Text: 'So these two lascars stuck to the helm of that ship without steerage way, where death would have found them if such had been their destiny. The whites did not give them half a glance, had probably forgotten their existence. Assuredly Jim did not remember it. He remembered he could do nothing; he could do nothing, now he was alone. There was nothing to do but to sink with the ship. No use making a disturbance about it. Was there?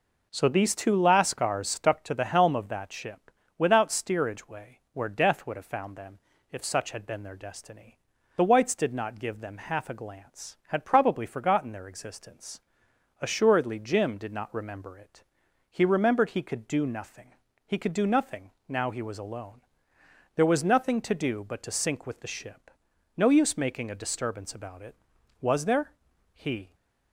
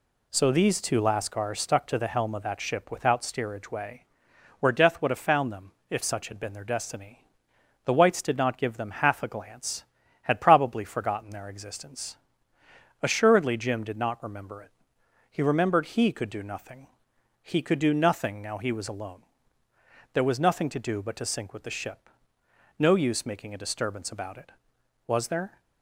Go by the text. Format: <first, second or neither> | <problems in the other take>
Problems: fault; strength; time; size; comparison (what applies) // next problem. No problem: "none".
second | pauses between "ship" and "without"; slight; at 3.3 s; 0.26 s long // pauses between "them" and "if"; slight; at 6.1 s; 0.32 s long; slight in the second // goes on to say "He"; slight; from 26.3 s on; 0.40 s long